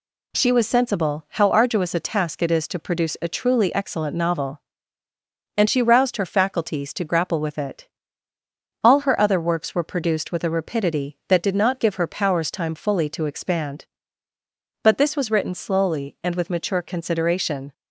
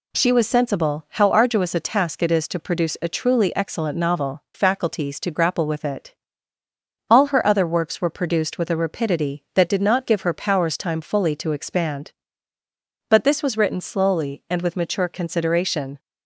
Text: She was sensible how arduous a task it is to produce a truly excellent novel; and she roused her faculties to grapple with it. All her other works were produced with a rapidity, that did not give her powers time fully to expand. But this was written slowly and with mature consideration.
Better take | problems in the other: first | skips "and she roused her"; at 4.4 s

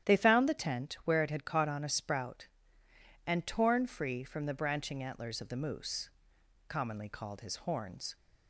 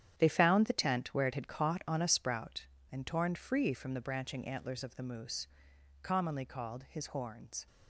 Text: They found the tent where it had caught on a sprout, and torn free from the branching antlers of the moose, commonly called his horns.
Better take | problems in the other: first | gets quieter; strong; throughout; 10.5 dB // starts louder than the rest; strong; until 1.1 s; 9.5 dB; strong in the first

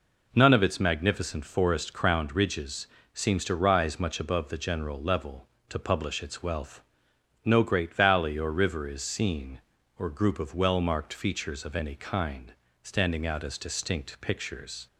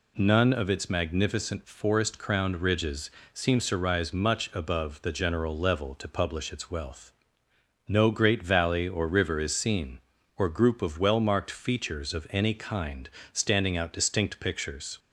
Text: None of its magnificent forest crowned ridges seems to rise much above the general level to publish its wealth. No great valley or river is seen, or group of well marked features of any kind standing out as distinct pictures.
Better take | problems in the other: first | pauses between "ridges" and "seems"; slight; at 3.1 s; 0.22 s long; slight in the first // pauses between "kind" and "standing"; slight; at 13.0 s; 0.24 s long; slight in the first // skips "as"; at 13.9 s

